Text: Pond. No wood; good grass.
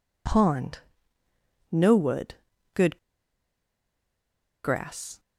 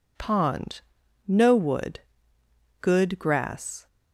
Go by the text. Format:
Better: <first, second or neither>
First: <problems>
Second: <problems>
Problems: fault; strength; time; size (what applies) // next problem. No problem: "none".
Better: second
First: pauses between "good" and "grass"; strong; at 2.9 s; 1.6 s long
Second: none